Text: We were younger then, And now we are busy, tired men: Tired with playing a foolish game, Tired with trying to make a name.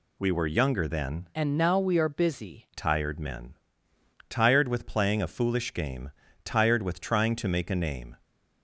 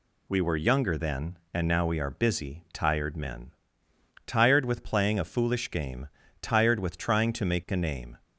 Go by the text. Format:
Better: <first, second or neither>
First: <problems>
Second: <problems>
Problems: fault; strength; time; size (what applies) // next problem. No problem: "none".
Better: second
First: changes voice from "And" to "busy"; from 1.3 to 2.6 s; 1.3 s long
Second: none